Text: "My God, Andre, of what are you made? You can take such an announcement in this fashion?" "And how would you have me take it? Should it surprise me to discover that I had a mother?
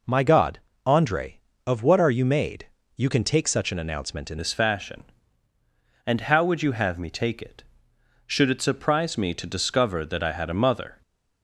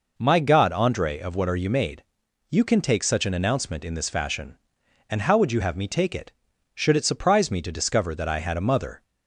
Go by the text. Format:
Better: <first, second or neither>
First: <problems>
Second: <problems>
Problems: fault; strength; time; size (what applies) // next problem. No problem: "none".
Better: second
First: changes voice at "this"; from 4.3 s on; 6.7 s long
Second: none